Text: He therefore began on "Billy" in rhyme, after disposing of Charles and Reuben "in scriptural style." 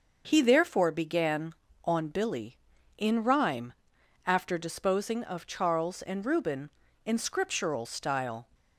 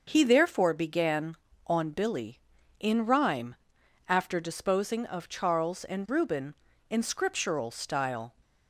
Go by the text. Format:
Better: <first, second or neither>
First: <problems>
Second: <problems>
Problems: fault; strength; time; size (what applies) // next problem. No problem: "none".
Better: neither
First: starts louder than the rest; until 1.2 s; 6 dB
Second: starts louder than the rest; until 1.0 s; 6.5 dB